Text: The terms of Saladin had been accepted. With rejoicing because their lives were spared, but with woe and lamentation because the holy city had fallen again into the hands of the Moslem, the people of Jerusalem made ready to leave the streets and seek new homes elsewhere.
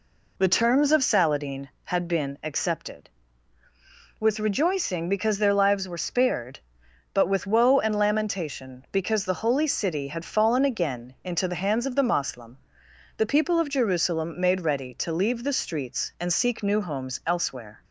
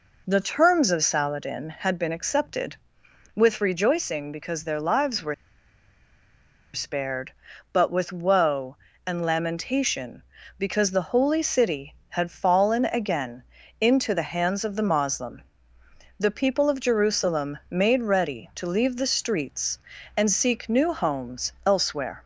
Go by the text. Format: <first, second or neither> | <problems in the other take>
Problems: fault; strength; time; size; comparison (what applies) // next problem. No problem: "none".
first | pauses between "were" and "spared"; strong; at 5.3 s; 1.3 s long // pauses between "again" and "into"; slight; at 13.4 s; 0.36 s long